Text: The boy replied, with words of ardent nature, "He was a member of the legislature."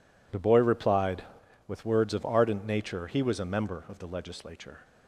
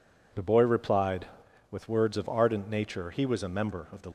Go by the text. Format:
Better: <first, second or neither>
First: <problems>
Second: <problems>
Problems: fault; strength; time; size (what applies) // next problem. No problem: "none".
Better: first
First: none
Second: stops before "legislature"; at 4.0 s